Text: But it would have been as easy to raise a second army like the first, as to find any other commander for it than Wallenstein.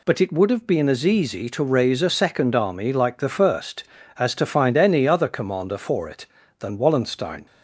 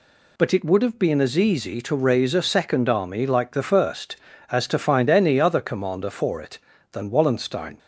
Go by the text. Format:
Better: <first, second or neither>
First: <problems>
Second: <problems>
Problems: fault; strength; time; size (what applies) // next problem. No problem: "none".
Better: neither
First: none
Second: none